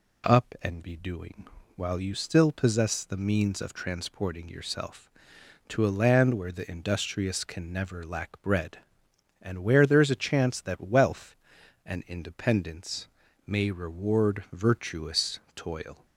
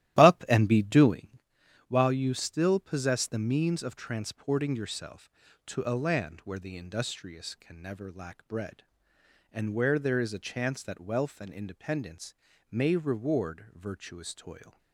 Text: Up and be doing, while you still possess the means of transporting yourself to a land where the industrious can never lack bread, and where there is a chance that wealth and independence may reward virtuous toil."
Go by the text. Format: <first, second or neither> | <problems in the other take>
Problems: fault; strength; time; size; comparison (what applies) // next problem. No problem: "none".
first | starts louder than the rest; strong; until 1.5 s; 13.5 dB // pauses between "independence" and "may"; at 12.3 s; 0.38 s long; also in the first